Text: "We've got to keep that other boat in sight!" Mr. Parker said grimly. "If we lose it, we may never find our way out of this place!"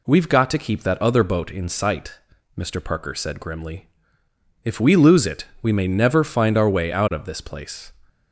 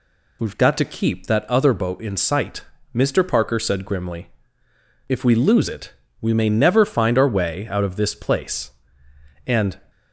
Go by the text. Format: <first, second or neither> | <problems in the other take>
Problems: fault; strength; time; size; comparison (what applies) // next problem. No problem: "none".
first | goes on to say "And"; slight; from 9.4 s on; 0.34 s long